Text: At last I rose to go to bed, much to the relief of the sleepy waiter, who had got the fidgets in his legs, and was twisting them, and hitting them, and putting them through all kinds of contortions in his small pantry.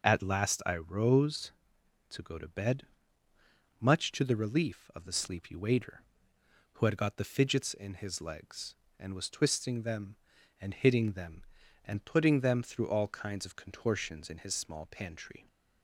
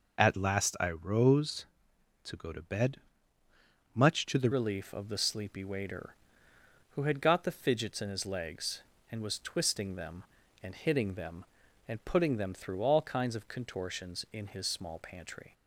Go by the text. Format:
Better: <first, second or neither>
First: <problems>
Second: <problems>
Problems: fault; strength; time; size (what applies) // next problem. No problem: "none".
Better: first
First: none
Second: changes voice at "relief"; from 4.5 s on; 11.0 s long